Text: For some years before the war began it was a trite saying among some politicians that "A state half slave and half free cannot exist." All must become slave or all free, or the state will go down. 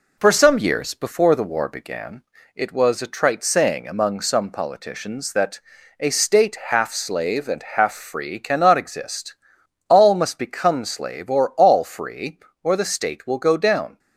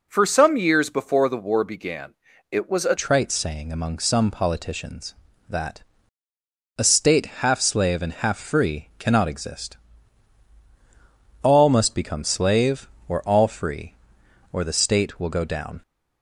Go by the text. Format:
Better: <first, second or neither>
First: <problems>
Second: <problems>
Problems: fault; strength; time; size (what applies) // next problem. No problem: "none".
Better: first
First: pauses between "began" and "it"; slight; at 2.2 s; 0.32 s long // pauses between "that" and "A"; at 5.6 s; 0.40 s long // pauses between "state" and "half"; slight; at 6.5 s; 0.16 s long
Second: pauses between "began" and "it"; slight; at 2.1 s; 0.34 s long // changes voice at "trite"; from 2.9 s on; 12.9 s long // pauses between "that" and "A"; noticeable; at 5.8 s; 0.96 s long // pauses between "state" and "half"; slight; at 7.2 s; 0.16 s long